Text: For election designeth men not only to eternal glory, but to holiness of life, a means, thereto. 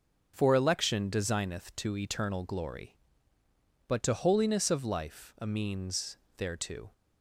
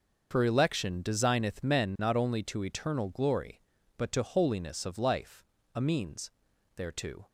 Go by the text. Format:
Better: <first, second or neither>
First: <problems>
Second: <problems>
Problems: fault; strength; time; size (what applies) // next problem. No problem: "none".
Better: second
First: starts louder than the rest; noticeable; until 1.3 s; 6 dB // skips "men not only"; at 1.7 s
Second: starts louder than the rest; until 1.3 s; 6 dB